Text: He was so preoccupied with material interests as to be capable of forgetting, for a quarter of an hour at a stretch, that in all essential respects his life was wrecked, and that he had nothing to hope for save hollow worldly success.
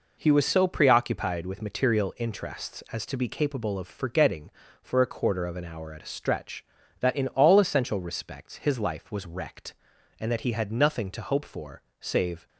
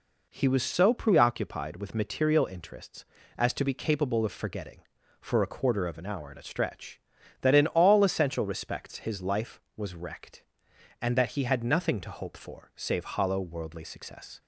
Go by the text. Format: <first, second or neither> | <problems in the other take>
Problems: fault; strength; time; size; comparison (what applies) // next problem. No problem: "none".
second | pauses between "for" and "save"; slight; at 11.8 s; 0.18 s long // stops before "hollow worldly success"; at 12.4 s